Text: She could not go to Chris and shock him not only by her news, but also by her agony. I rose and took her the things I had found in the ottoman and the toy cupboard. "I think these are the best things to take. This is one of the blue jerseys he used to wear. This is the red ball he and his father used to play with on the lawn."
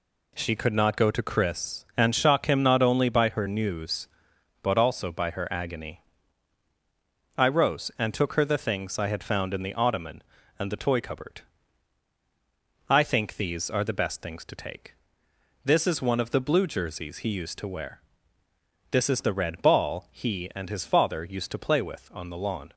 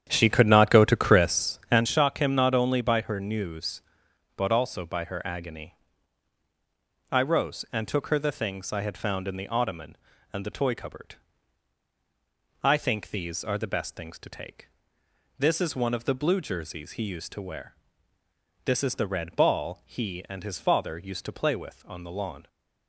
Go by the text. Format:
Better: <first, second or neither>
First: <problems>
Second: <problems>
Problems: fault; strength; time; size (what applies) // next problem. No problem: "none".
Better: first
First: none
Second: starts louder than the rest; strong; until 1.8 s; 9.5 dB